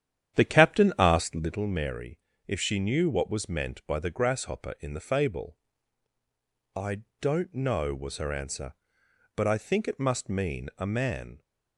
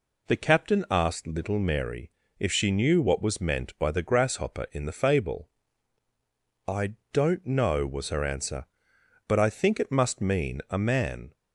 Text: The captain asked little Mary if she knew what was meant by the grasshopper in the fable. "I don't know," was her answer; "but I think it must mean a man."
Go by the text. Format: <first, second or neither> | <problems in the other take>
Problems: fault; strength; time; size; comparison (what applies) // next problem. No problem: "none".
second | starts louder than the rest; strong; until 1.6 s; 10 dB // pauses between "Mary" and "if"; slight; at 2.1 s; 0.30 s long; slight in the second // pauses between "I" and "don't"; slight; at 7.0 s; 0.18 s long; slight in the second